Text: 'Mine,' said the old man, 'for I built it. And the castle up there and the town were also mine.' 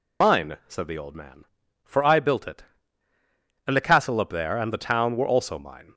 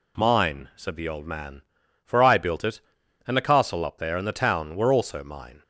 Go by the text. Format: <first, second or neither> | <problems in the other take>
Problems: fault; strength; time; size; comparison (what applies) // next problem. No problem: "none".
second | loses the start of "Mine"; at 0.2 s; 50 ms